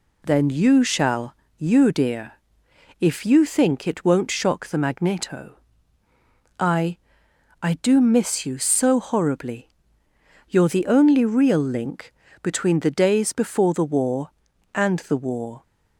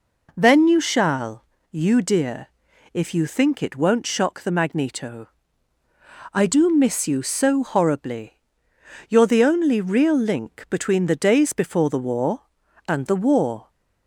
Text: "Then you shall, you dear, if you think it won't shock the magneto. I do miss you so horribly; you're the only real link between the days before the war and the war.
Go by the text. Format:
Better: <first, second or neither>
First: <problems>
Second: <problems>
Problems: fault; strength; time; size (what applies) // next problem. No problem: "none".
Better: second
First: says "I" twice; at 7.6 s // pauses between "link" and "between"; slight; at 12.1 s; 0.28 s long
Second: none